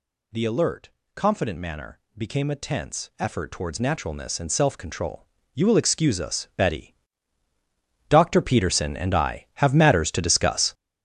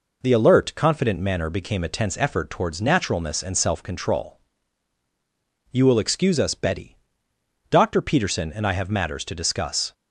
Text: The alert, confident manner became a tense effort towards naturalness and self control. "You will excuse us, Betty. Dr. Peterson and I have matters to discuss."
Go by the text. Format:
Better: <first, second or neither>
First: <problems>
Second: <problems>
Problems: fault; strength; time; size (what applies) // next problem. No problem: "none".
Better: second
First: gets louder; strong; throughout; 10 dB // pauses between "manner" and "became"; slight; at 1.9 s; 0.18 s long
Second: none